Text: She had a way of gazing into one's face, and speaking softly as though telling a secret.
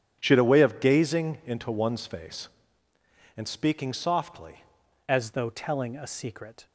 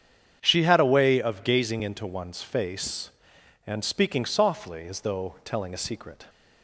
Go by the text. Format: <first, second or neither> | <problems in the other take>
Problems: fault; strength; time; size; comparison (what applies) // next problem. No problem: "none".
second | starts louder than the rest; strong; until 1.2 s; 9 dB; strong in the second // changes voice at "as"; from 5.0 s on; 1.6 s long